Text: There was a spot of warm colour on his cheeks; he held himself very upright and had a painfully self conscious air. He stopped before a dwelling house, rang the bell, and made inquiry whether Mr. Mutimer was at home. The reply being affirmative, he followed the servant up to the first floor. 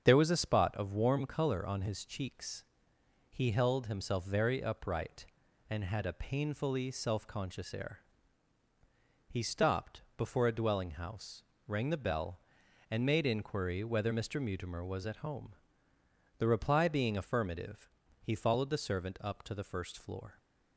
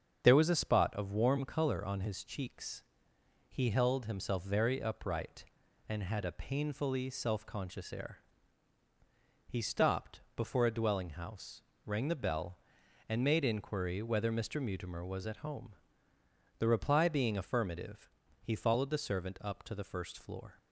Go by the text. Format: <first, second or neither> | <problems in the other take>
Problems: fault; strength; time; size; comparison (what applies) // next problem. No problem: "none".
neither | starts louder than the rest; strong; the same in both